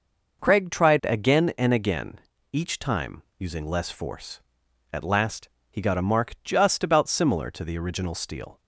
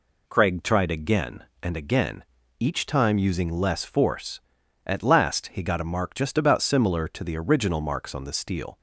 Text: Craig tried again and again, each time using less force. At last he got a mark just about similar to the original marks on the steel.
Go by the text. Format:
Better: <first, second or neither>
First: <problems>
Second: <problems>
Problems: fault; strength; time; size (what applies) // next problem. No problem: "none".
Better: second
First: pauses between "time" and "using"; slight; at 3.2 s; 0.18 s long // pauses between "last" and "he"; slight; at 5.4 s; 0.22 s long // skips "marks on the"; at 8.1 s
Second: none